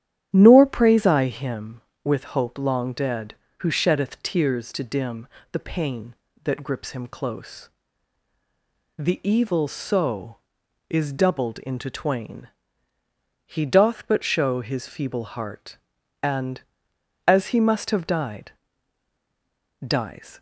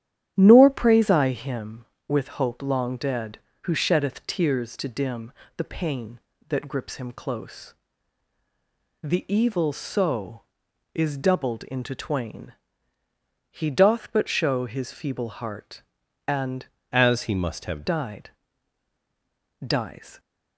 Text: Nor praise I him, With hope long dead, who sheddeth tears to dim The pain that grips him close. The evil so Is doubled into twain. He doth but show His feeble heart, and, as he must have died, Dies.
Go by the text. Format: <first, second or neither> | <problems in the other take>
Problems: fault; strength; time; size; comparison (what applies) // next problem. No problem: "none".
first | starts louder than the rest; strong; until 1.3 s; 11 dB; strong in the first // pauses between "dim" and "The"; slight; at 5.3 s; 0.24 s long; slight in the first // changes voice from "as" to "have"; from 16.9 to 17.8 s; 0.9 s long